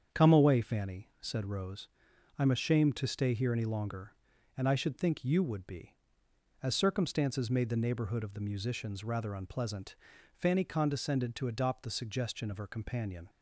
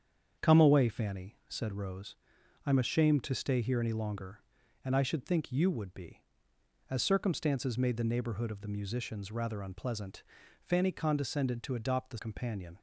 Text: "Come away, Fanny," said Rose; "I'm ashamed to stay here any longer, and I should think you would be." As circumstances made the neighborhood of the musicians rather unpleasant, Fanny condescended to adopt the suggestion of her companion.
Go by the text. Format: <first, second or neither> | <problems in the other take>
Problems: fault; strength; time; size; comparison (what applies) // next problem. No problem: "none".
first | starts louder than the rest; strong; until 1.5 s; 7.5 dB; strong in the first // skips "suggestion of her"; at 12.1 s